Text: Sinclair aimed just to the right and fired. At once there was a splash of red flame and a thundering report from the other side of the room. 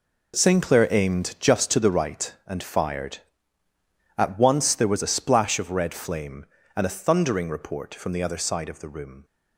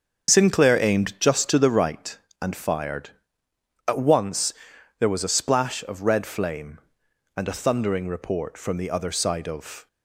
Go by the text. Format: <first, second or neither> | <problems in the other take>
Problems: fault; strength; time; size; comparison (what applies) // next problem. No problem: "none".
first | starts louder than the rest; until 1.3 s; 7 dB // pauses between "once" and "there"; noticeable; at 4.5 s; 0.46 s long // stops before "the room"; at 9.8 s